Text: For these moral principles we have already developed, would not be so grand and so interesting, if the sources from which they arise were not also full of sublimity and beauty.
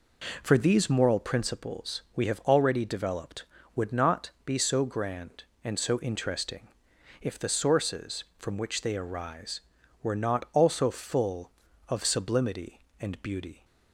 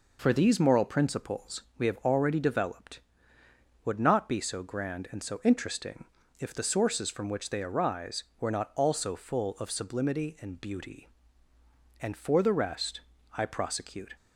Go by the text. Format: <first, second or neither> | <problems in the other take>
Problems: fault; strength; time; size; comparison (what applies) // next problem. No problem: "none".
first | pauses between "principles" and "we"; slight; at 1.6 s; 0.16 s long // goes on to say "And for the rest I prosecute"; strong; from 12.0 s on; 2.1 s long